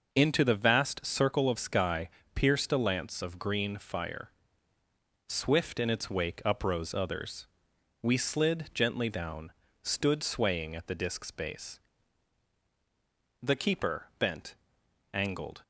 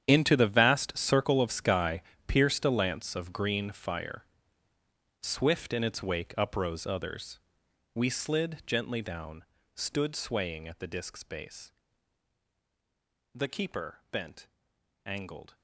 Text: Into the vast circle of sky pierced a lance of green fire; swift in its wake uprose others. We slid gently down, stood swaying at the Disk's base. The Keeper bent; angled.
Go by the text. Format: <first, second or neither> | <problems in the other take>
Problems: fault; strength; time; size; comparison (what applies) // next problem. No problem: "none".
first | gets quieter; strong; throughout; 15 dB // pauses between "sky" and "pierced"; slight; at 2.0 s; 0.26 s long; slight in the first